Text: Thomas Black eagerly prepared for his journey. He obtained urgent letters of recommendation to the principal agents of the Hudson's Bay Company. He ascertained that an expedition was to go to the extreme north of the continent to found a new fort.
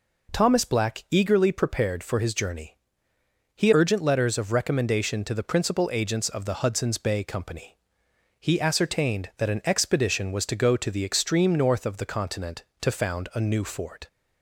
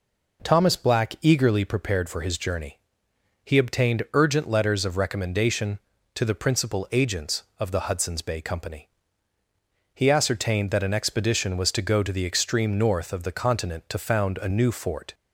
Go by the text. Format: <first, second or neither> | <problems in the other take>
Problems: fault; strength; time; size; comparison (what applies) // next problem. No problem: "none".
second | skips "obtained"; at 3.7 s